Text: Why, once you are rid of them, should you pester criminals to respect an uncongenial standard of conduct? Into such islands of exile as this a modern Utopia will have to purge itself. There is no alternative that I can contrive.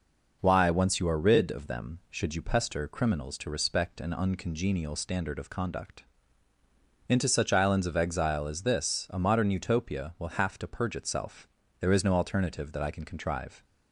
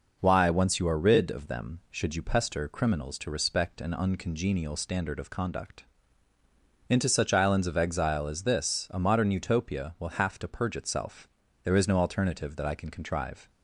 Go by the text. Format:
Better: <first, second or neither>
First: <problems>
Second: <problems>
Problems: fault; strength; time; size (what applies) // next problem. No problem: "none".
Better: neither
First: none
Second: none